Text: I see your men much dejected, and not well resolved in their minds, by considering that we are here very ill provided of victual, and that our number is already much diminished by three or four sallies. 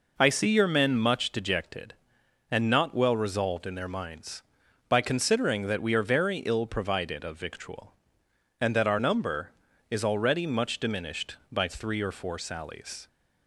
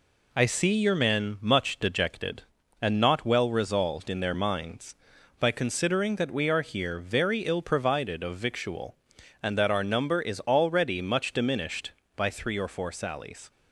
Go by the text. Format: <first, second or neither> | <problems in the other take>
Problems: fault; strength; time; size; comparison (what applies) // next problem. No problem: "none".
second | skips "here"; at 6.0 s